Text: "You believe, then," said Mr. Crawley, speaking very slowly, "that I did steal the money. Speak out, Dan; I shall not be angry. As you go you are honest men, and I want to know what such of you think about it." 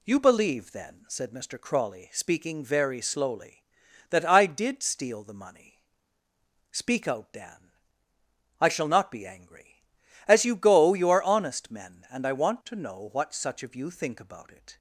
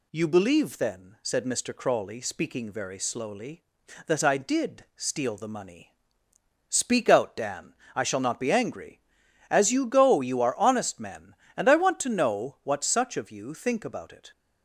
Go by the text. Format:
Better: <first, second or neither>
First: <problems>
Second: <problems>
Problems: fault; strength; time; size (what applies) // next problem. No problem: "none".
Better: neither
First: none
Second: none